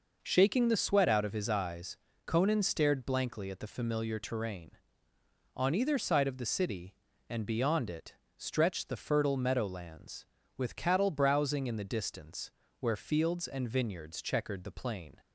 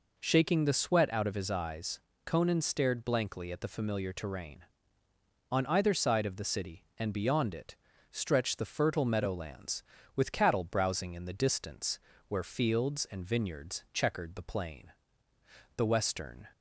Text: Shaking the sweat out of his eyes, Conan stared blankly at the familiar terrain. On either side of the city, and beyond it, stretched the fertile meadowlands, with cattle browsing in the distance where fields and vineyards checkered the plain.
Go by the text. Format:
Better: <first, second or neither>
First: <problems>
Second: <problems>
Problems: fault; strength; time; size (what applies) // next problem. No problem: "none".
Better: first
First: pauses between "distance" and "where"; slight; at 12.4 s; 0.30 s long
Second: pauses between "distance" and "where"; slight; at 11.9 s; 0.30 s long // goes on to say "The western"; noticeable; from 15.7 s on; 0.72 s long